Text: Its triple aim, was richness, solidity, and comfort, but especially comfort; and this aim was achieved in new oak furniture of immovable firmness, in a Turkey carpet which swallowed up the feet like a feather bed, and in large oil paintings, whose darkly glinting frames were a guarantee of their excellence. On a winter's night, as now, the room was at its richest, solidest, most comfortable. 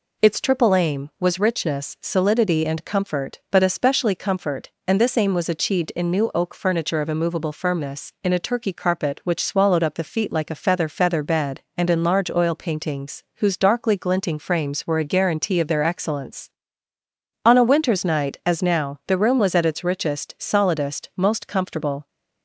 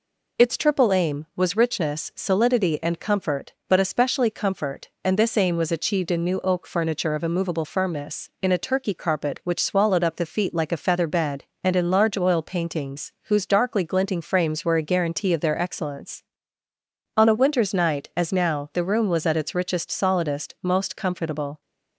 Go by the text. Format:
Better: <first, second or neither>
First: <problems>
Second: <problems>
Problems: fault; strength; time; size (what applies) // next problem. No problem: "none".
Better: second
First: says "feather" twice; at 10.8 s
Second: none